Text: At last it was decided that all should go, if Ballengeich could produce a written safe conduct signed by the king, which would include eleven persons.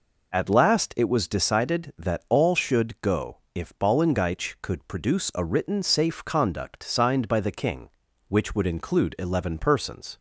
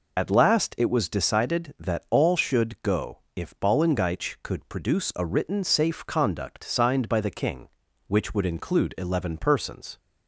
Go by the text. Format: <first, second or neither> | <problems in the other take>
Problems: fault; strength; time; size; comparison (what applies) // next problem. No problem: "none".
first | loses the start of "At"; at 0.1 s; 30 ms